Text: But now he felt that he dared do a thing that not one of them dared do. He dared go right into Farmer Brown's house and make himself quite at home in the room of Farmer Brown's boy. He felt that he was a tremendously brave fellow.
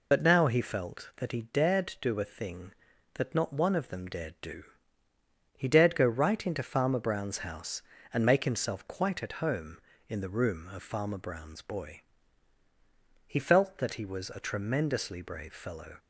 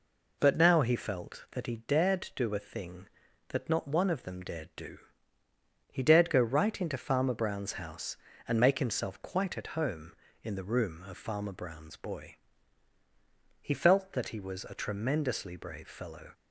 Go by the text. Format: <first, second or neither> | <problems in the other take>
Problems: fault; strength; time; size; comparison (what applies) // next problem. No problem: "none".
second | loses the start of "But"; at 0.1 s; 65 ms